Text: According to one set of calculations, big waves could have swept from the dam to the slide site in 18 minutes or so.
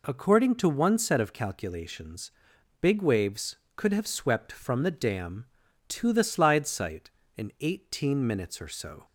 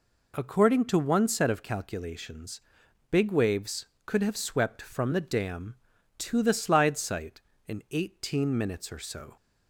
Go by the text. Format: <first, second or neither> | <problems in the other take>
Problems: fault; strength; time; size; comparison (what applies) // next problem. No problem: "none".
neither | none